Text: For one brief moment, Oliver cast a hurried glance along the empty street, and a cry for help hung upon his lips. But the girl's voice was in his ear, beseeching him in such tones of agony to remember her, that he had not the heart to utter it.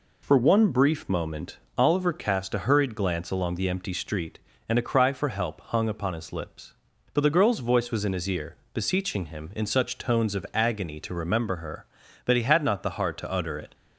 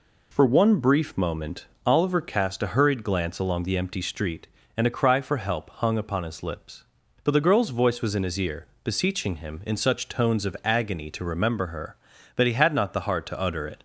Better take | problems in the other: neither | none

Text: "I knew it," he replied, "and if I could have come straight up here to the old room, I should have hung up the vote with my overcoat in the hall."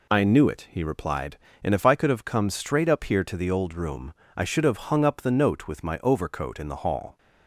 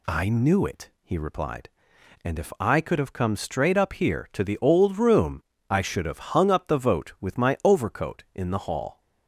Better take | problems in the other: second | says "note" for "vote"; at 5.3 s

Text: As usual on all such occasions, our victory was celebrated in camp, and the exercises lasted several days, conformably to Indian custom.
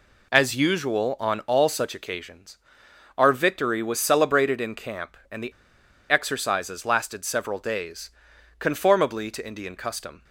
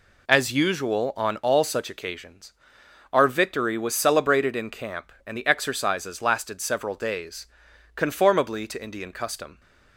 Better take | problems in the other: second | pauses between "the" and "exercises"; noticeable; at 5.5 s; 0.57 s long

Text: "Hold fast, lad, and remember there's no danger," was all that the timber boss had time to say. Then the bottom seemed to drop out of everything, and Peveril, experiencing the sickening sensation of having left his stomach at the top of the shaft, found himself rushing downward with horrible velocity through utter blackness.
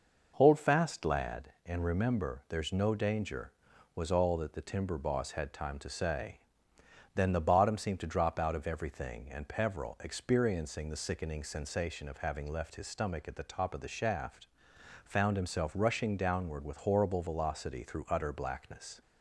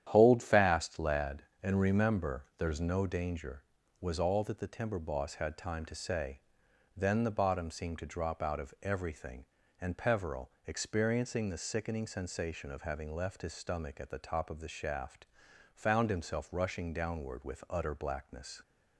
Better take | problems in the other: first | starts louder than the rest; strong; until 1.1 s; 10 dB // skips "horrible velocity through"; at 17.6 s

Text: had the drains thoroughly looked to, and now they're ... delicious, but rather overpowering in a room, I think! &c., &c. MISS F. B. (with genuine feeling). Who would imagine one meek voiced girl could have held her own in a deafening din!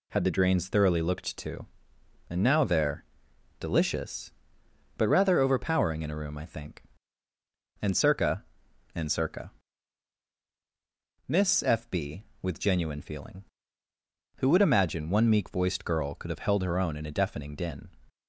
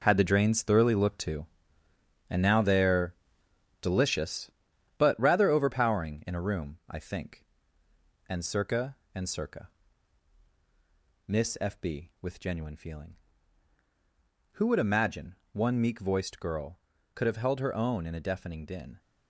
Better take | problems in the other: first | gets quieter; strong; throughout; 9.5 dB // pauses between "imagine" and "one"; slight; at 15.3 s; 0.16 s long

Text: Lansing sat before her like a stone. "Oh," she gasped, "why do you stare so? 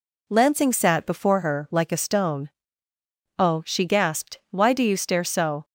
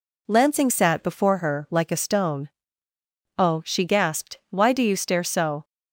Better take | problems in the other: neither | none

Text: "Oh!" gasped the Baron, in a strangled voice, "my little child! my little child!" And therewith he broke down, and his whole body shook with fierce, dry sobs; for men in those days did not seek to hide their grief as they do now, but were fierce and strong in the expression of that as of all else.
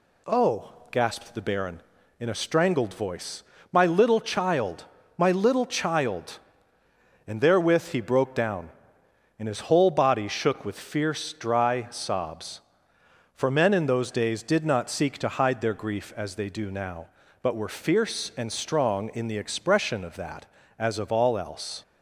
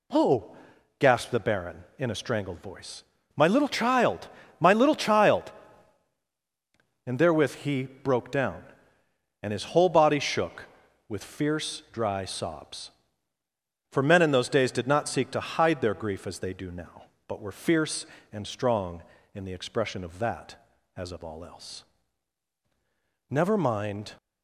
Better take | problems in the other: first | goes on to say "Never mind"; noticeable; from 23.2 s on; 0.86 s long

